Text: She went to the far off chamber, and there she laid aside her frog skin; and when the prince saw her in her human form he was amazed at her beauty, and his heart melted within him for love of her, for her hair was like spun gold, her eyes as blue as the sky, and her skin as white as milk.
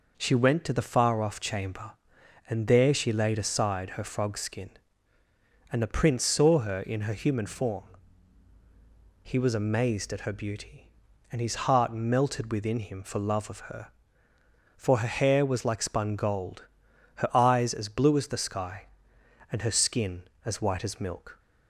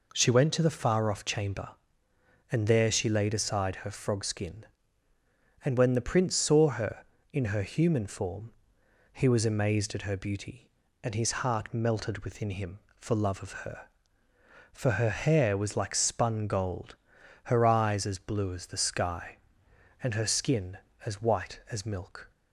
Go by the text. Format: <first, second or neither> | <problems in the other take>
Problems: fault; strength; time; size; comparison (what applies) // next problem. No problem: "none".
second | skips "when"; at 5.8 s // pauses between "form" and "he"; strong; at 7.8 s; 1.4 s long; noticeable in the second